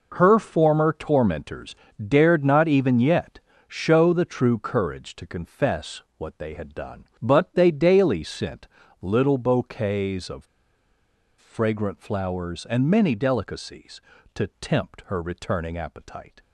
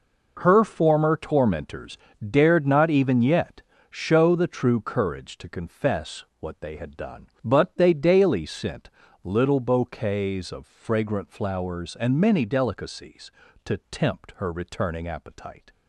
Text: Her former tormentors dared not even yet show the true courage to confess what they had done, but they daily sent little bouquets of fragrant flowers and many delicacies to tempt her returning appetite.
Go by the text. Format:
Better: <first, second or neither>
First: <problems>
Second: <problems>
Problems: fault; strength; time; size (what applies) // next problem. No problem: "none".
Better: second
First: pauses between "tormentors" and "dared"; slight; at 1.7 s; 0.32 s long // pauses between "yet" and "show"; slight; at 3.3 s; 0.28 s long // pauses between "confess" and "what"; slight; at 6.0 s; 0.16 s long // pauses between "sent" and "little"; slight; at 8.6 s; 0.34 s long // pauses between "of" and "fragrant"; noticeable; at 10.4 s; 0.93 s long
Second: pauses between "tormentors" and "dared"; slight; at 1.9 s; 0.32 s long // pauses between "yet" and "show"; slight; at 3.6 s; 0.28 s long // pauses between "confess" and "what"; slight; at 6.2 s; 0.16 s long // pauses between "sent" and "little"; slight; at 8.8 s; 0.34 s long